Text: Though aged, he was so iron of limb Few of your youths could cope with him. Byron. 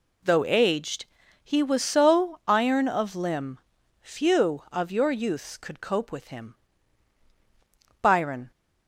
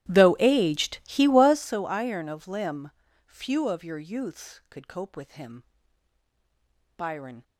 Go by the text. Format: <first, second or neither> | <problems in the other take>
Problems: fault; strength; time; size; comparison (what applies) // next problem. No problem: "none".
first | starts louder than the rest; strong; until 1.7 s; 13.5 dB // pauses between "limb" and "Few"; slight; at 2.9 s; 0.36 s long; also in the first